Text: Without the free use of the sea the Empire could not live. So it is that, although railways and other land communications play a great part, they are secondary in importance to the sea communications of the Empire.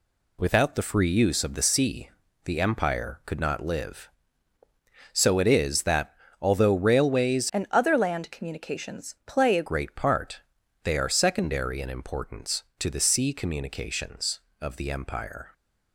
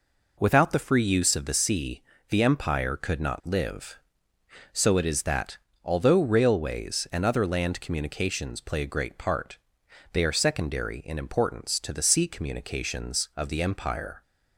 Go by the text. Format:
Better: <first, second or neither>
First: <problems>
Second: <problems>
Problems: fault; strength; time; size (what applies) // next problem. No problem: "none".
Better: second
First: pauses between "sea" and "the"; slight; at 2.0 s; 0.36 s long // changes voice from "and" to "a"; from 7.5 to 9.6 s; 2.1 s long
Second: pauses between "sea" and "the"; slight; at 2.0 s; 0.28 s long